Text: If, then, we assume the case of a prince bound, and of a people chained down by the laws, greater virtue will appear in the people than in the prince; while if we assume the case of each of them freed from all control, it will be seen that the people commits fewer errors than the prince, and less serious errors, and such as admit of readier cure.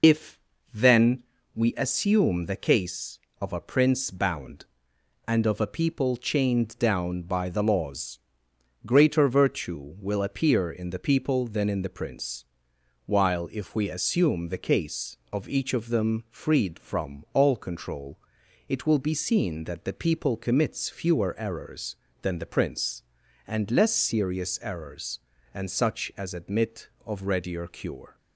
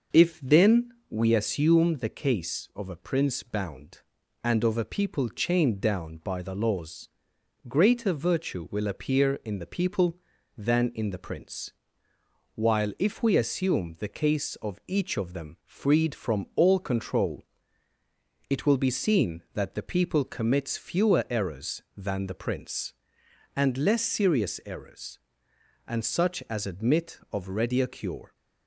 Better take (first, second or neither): second